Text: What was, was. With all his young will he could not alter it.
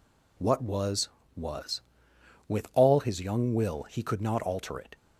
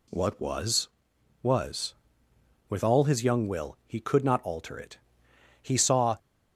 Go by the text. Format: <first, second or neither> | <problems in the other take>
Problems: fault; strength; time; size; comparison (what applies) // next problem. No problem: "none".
first | goes on to say "He saw"; from 5.6 s on; 0.54 s long